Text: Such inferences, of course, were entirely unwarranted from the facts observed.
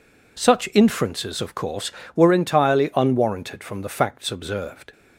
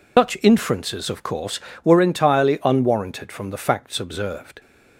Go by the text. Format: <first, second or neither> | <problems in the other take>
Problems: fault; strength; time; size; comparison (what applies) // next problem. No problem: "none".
first | loses the start of "Such"; at 0.1 s; 115 ms